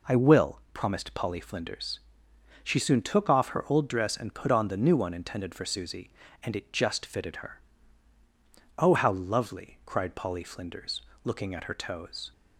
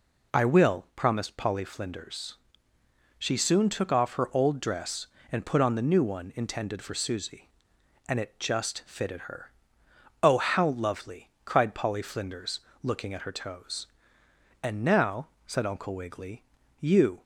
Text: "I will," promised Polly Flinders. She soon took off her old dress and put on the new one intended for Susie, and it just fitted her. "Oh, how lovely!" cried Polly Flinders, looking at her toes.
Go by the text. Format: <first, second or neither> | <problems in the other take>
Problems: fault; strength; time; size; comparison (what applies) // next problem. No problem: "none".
first | goes on to say "And now said Uncle Wiggily you"; strong; from 14.6 s on; 2.6 s long